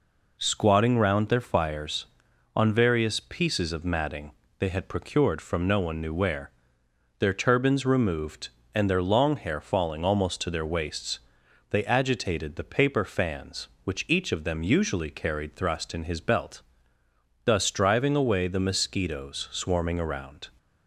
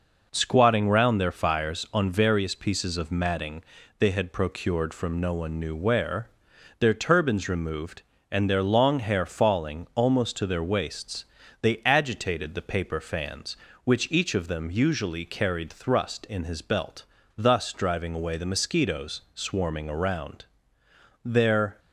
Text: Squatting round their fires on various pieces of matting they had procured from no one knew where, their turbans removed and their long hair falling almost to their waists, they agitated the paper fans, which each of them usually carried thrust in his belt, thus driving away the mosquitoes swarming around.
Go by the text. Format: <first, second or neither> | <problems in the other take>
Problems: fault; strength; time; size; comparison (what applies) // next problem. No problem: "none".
first | pauses between "matting" and "they"; slight; at 3.6 s; 0.34 s long; slight in the first // goes on to say "Their"; from 21.2 s on; 0.54 s long